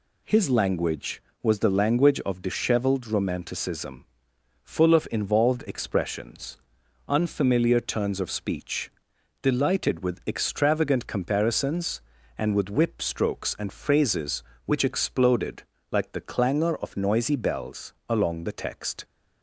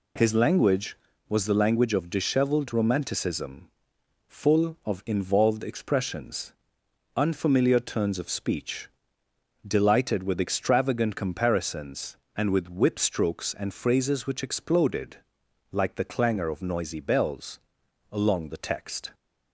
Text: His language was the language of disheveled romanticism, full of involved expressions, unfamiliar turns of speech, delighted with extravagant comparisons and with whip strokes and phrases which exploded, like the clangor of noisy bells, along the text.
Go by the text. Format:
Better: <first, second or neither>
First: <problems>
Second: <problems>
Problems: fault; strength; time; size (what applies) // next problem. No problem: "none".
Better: neither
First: none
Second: none